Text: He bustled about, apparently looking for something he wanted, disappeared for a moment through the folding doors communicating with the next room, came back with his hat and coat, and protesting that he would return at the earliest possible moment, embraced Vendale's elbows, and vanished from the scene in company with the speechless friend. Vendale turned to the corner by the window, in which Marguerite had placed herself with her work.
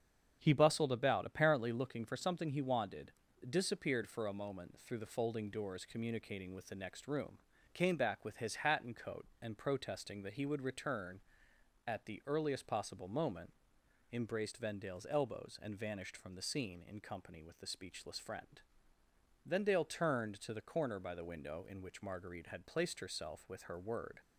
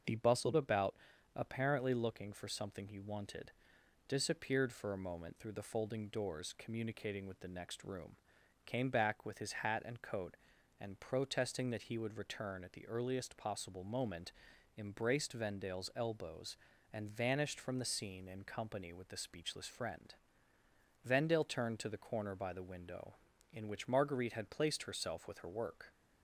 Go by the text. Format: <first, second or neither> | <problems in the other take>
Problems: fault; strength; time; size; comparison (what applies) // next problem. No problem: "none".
second | starts louder than the rest; strong; until 1.4 s; 7.5 dB; also in the second // says "word" for "work"; at 23.7 s